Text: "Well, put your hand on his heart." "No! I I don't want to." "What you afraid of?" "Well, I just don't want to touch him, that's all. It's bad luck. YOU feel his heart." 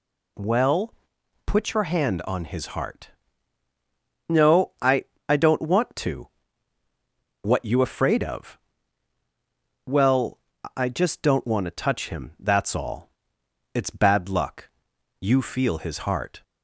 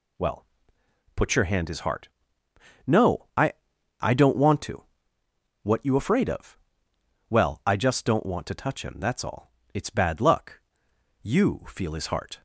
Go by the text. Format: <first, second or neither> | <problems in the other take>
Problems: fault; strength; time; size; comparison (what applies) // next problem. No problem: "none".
first | skips "on"; at 1.6 s // pauses between "I" and "I"; noticeable; at 3.5 s; 0.46 s long; slight in the first